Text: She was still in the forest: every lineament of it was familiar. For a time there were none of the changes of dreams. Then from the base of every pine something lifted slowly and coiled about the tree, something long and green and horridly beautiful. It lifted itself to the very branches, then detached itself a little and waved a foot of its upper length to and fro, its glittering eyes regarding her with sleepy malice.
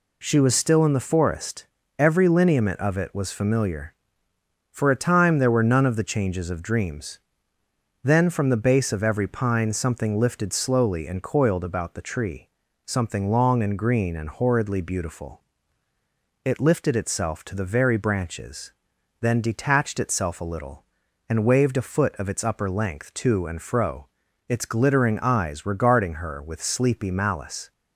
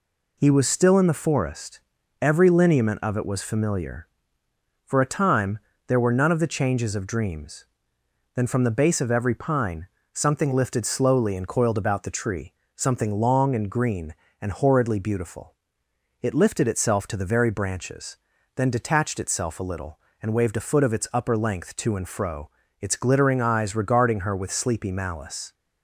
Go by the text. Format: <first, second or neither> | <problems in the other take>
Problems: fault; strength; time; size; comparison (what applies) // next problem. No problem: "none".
first | says "He" for "She"; at 0.3 s // pauses between "time" and "there"; slight; at 5.5 s; 0.30 s long // pauses between "pine" and "something"; slight; at 9.8 s; 0.26 s long